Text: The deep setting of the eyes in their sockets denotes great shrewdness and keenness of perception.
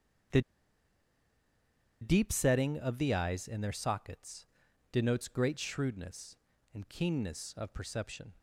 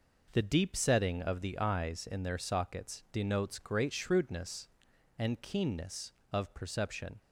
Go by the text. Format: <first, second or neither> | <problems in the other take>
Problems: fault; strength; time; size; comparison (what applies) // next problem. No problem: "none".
second | starts louder than the rest; strong; until 2.9 s; 7.5 dB // pauses between "The" and "deep"; strong; at 0.4 s; 1.6 s long // pauses between "sockets" and "denotes"; noticeable; at 4.4 s; 0.46 s long